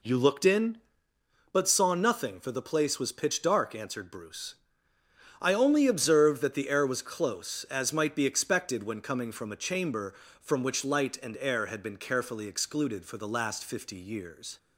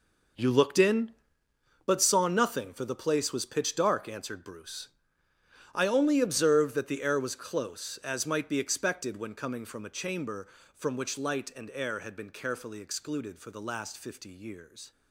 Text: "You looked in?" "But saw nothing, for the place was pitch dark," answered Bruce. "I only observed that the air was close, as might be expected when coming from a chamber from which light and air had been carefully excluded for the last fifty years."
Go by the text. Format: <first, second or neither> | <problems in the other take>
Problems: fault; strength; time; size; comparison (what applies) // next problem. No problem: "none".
first | gets quieter; strong; throughout; 12 dB